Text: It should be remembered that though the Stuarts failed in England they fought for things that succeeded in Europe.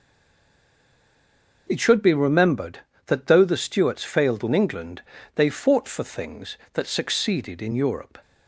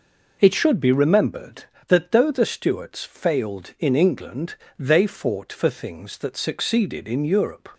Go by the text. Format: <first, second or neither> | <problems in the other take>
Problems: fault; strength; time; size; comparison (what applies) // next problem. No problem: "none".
second | stays silent before the first word; noticeable; until 1.6 s; 1.6 s long // pauses between "England" and "they"; slight; at 5.0 s; 0.34 s long; slight in the second